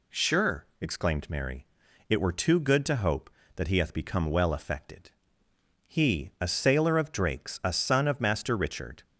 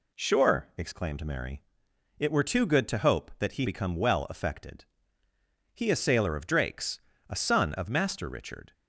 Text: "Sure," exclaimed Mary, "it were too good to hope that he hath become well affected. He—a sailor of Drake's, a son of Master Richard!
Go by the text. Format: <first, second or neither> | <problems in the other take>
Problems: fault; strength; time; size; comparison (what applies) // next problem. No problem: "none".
first | skips "hath"; at 3.6 s